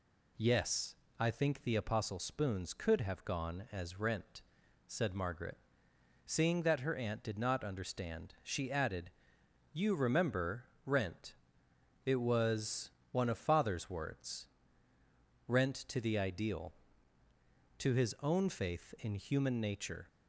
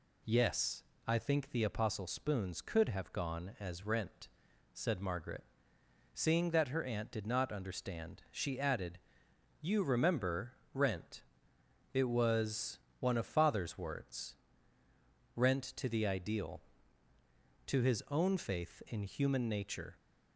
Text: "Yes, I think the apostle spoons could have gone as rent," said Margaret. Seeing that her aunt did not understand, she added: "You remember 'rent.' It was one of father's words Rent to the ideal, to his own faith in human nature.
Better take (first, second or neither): neither